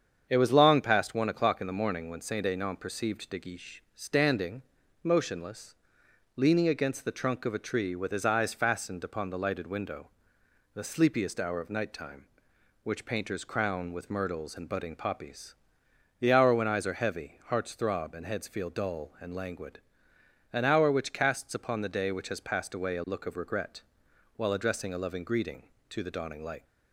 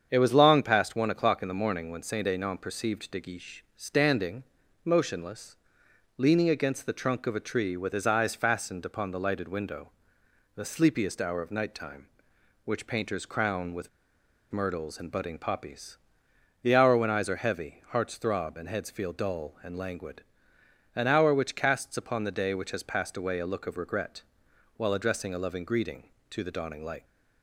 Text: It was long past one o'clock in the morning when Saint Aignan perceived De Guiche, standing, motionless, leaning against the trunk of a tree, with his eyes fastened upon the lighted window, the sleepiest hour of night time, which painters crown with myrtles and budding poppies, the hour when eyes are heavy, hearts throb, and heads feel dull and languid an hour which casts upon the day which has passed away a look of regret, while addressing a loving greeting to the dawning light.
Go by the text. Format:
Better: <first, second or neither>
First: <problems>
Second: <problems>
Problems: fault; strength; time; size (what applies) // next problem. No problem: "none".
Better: first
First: starts louder than the rest; strong; until 1.3 s; 7.5 dB // pauses between "languid" and "an"; noticeable; at 19.7 s; 0.74 s long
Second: starts louder than the rest; strong; until 1.1 s; 7.5 dB // pauses between "with" and "myrtles"; noticeable; at 13.8 s; 0.63 s long // pauses between "languid" and "an"; noticeable; at 20.2 s; 0.74 s long